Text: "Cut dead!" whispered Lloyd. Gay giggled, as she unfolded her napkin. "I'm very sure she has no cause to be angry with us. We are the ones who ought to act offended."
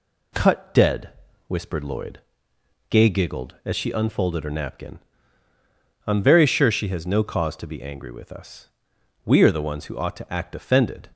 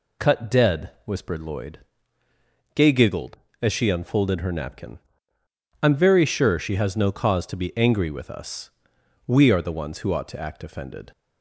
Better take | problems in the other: neither | none

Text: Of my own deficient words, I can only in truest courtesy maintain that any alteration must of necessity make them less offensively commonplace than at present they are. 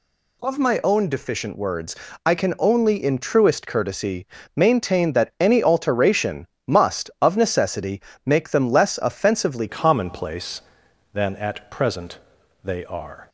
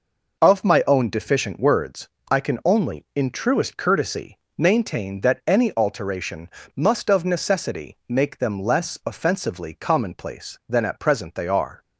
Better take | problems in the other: second | pauses between "courtesy" and "maintain"; slight; at 4.2 s; 0.30 s long; slight in the second // pauses between "alteration" and "must"; slight; at 6.4 s; 0.18 s long; slight in the second // pauses between "necessity" and "make"; slight; at 8.0 s; 0.24 s long // changes voice at "commonplace"; from 9.6 s on; 3.6 s long // pauses between "present" and "they"; noticeable; at 12.1 s; 0.48 s long

